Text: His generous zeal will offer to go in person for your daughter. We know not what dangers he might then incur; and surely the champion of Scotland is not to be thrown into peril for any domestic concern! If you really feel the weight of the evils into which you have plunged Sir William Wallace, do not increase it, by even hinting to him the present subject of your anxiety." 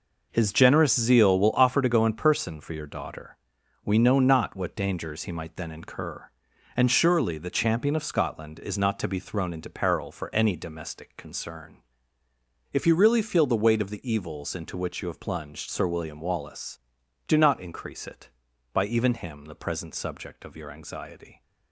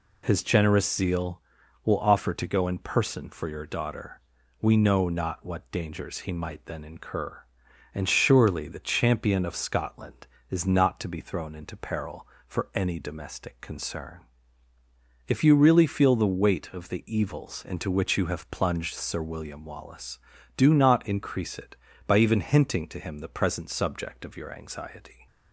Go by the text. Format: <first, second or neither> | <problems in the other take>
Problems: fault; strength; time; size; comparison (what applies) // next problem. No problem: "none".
second | skips "hinting to"; at 19.1 s